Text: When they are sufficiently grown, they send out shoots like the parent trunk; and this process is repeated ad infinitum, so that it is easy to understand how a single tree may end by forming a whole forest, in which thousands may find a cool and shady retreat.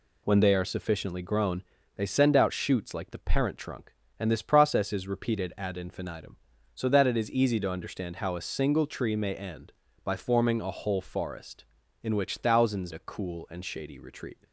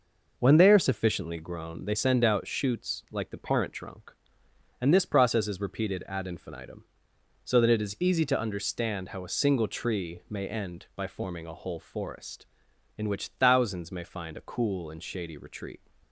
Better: second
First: skips "may find"; at 12.9 s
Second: none

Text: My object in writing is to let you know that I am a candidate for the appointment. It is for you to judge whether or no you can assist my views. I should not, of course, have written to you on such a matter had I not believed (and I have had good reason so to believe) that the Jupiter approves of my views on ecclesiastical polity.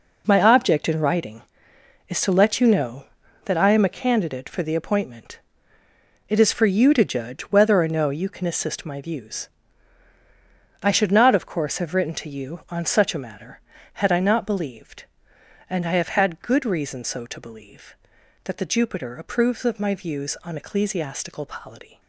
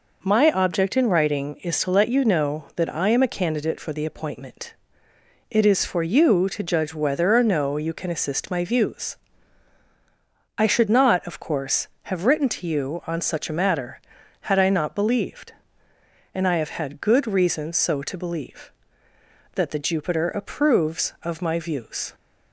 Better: first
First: none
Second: stops before "on ecclesiastical polity"; at 22.1 s

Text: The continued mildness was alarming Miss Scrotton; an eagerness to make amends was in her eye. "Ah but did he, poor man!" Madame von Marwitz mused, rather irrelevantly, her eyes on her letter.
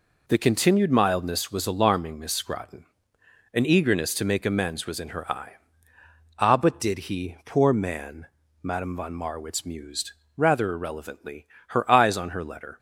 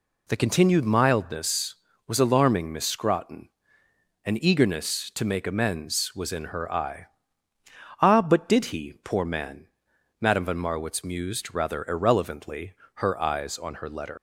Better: first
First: none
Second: leaves "letter" unfinished; at 14.1 s; 150 ms

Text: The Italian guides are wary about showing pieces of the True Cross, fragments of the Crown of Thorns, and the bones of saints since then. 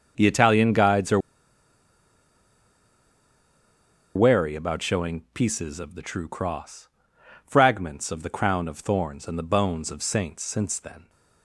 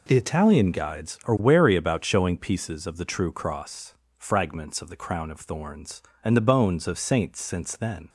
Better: second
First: starts louder than the rest; until 1.1 s; 6 dB // pauses between "are" and "wary"; strong; at 1.1 s; 2.9 s long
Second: none

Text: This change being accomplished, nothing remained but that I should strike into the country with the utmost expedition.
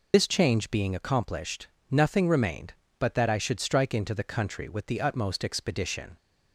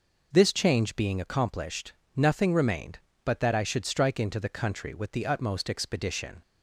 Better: second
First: loses the start of "This"; at 0.1 s; 70 ms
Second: none

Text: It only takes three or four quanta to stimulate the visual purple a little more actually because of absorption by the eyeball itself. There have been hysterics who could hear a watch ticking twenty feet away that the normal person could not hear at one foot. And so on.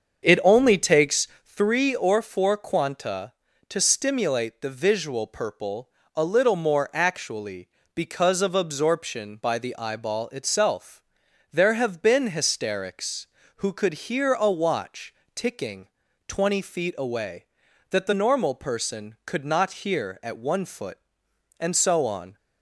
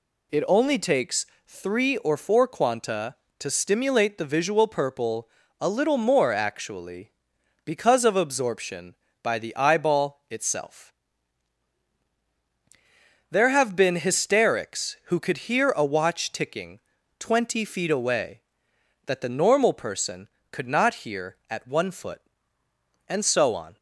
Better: second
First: starts louder than the rest; until 1.7 s; 7 dB // pauses between "takes" and "three"; slight; at 1.2 s; 0.18 s long // pauses between "purple" and "a"; slight; at 5.8 s; 0.26 s long // pauses between "watch" and "ticking"; slight; at 15.1 s; 0.22 s long // pauses between "ticking" and "twenty"; at 15.8 s; 0.38 s long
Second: pauses between "takes" and "three"; slight; at 1.2 s; 0.20 s long // pauses between "purple" and "a"; slight; at 5.2 s; 0.32 s long // pauses between "ticking" and "twenty"; at 16.8 s; 0.38 s long

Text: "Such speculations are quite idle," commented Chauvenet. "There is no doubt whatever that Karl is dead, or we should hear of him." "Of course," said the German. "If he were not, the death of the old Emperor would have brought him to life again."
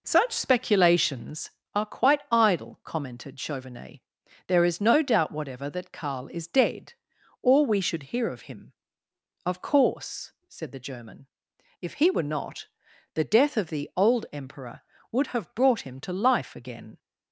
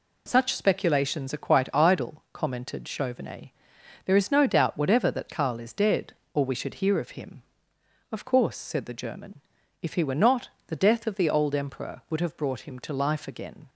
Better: second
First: starts louder than the rest; noticeable; until 1.7 s; 4.5 dB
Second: none

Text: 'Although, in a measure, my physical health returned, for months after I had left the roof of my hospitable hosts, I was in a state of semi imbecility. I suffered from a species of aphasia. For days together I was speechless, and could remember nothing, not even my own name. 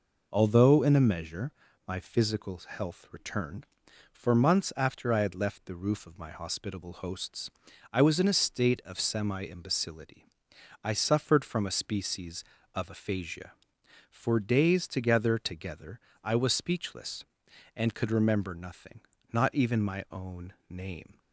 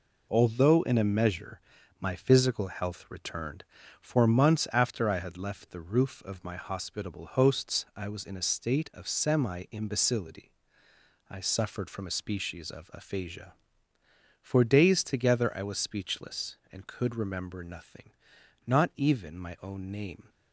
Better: second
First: says "together" twice; at 15.3 s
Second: none

